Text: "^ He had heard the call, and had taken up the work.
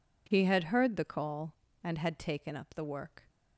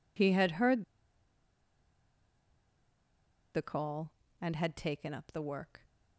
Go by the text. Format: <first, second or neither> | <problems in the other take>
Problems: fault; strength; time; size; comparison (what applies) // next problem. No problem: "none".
first | pauses between "heard" and "the"; strong; at 0.8 s; 2.7 s long